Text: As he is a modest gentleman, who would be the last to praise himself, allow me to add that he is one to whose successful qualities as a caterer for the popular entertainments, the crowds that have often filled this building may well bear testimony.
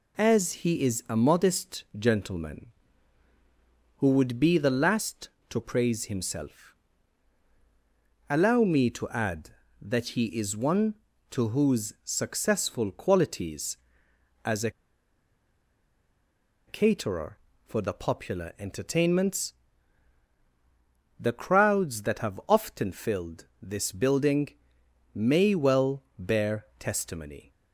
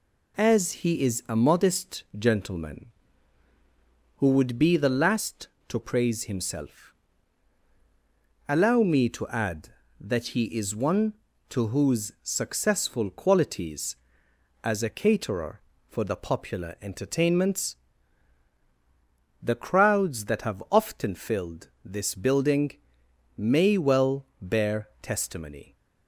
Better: second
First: pauses between "a" and "caterer"; strong; at 14.6 s; 1.9 s long // pauses between "building" and "may"; noticeable; at 24.4 s; 0.64 s long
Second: pauses between "building" and "may"; noticeable; at 22.7 s; 0.64 s long

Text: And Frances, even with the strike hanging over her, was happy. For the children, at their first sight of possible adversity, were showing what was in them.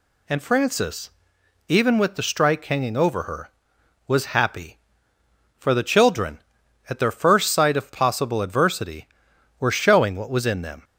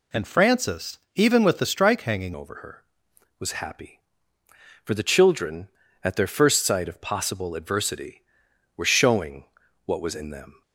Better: first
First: none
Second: changes voice at "over"; from 2.3 s on; 8.3 s long // pauses between "showing" and "what"; at 9.4 s; 0.42 s long

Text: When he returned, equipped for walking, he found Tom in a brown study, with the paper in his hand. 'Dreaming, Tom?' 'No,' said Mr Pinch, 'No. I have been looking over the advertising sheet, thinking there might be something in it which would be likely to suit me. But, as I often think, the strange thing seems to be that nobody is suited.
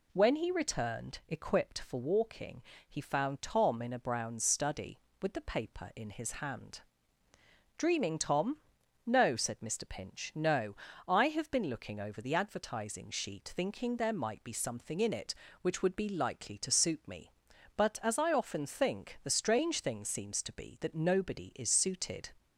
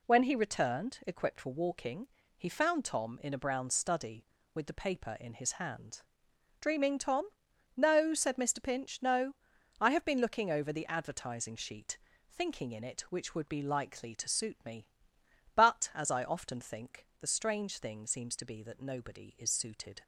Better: first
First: none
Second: skips "there might be something"; at 12.7 s

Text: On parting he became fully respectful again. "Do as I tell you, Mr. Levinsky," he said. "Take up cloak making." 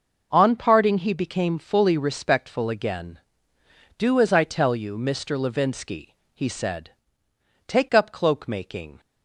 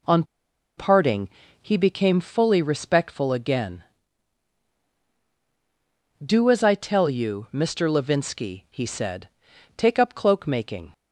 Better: first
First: none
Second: pauses between "On" and "parting"; noticeable; at 0.2 s; 0.54 s long // pauses between "parting" and "he"; slight; at 1.2 s; 0.32 s long

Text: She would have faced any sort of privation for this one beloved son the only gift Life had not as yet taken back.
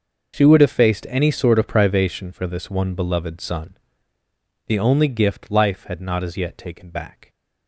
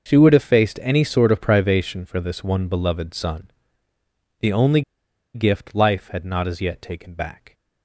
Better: first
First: starts louder than the rest; noticeable; until 1.4 s; 6 dB // pauses between "son" and "the"; noticeable; at 3.7 s; 0.88 s long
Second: starts louder than the rest; noticeable; until 1.1 s; 6 dB // pauses between "son" and "the"; noticeable; at 3.5 s; 0.88 s long // pauses between "only" and "gift"; noticeable; at 4.8 s; 0.53 s long

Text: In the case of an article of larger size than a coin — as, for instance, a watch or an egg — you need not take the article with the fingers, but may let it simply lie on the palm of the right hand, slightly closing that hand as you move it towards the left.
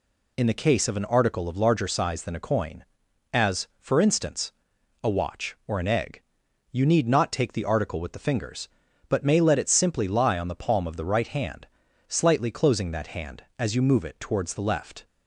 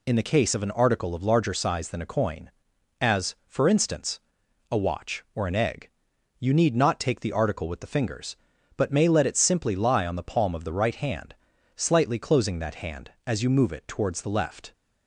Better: neither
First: none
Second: none

